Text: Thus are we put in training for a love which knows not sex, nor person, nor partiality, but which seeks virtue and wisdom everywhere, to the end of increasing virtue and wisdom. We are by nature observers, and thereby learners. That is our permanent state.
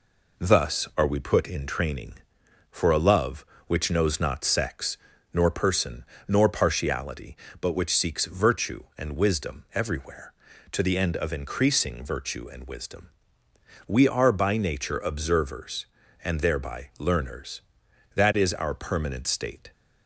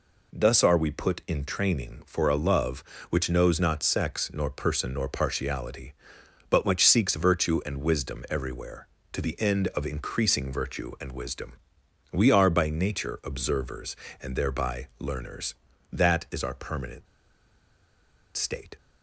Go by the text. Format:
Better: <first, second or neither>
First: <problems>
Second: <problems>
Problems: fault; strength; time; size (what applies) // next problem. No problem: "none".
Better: first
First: none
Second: pauses between "permanent" and "state"; strong; at 17.0 s; 1.3 s long